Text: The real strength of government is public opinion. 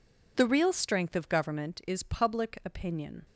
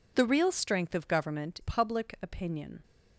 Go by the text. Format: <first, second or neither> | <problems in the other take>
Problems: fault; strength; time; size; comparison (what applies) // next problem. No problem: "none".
first | skips "is"; at 1.5 s